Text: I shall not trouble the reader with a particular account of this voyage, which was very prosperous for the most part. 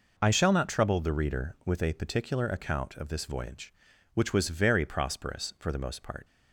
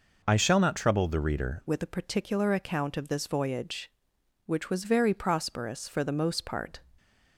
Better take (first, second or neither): first